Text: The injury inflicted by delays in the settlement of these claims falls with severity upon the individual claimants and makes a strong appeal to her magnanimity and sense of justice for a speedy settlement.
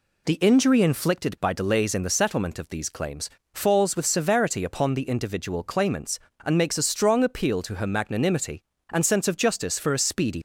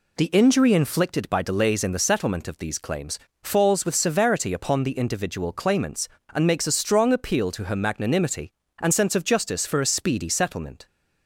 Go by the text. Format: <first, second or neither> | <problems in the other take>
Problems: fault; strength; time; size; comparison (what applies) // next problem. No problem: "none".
second | pauses between "claims" and "falls"; slight; at 3.3 s; 0.24 s long; slight in the second // stops before "settlement"; at 10.3 s